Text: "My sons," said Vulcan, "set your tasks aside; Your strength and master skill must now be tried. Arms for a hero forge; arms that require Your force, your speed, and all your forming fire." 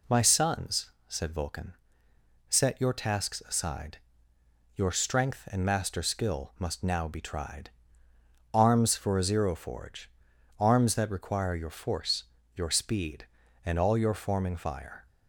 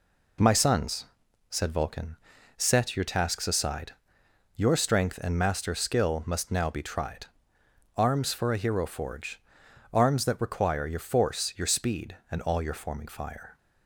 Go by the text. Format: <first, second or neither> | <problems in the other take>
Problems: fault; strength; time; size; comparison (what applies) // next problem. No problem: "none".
second | says "zero" for "hero"; at 9.2 s